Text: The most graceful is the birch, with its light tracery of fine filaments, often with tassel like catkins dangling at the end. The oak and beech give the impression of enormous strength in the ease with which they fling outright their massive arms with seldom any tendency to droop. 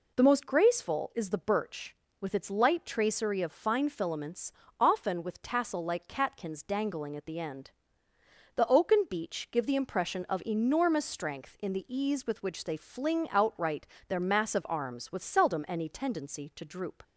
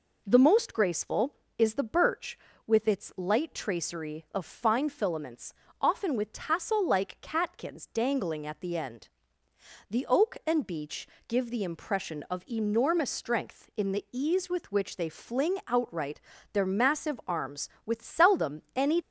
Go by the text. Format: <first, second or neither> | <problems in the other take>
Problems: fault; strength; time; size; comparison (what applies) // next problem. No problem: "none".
first | pauses between "beech" and "give"; slight; at 11.0 s; 0.18 s long // pauses between "outright" and "their"; slight; at 16.2 s; 0.32 s long; slight in the first // stops before "tendency to droop"; at 19.0 s